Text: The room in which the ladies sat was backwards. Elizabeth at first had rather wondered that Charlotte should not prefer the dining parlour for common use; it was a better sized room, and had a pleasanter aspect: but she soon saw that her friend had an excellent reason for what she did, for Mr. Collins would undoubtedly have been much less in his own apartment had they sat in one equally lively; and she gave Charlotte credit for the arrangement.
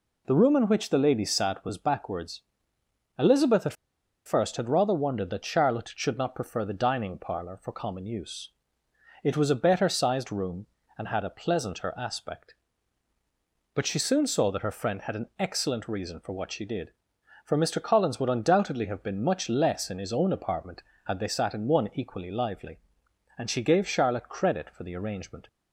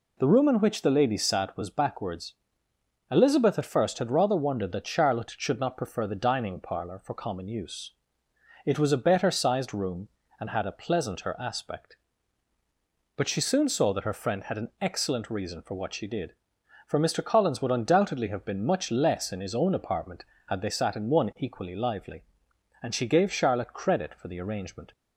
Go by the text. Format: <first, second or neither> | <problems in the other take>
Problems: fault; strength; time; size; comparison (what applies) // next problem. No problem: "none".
second | pauses between "at" and "first"; noticeable; at 3.7 s; 0.52 s long